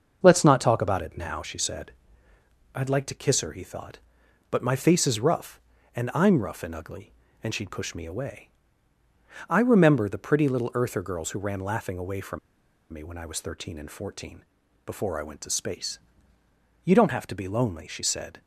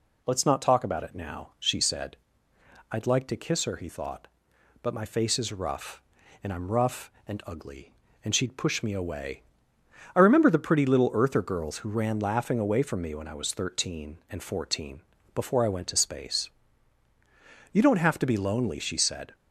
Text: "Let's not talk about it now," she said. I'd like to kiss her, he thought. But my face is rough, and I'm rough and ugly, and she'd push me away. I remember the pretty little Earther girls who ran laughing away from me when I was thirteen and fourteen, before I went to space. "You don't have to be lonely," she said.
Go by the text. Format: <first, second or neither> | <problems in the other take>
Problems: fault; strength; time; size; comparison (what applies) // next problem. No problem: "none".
second | starts louder than the rest; until 1.2 s; 6.5 dB // pauses between "from" and "me"; noticeable; at 12.3 s; 0.53 s long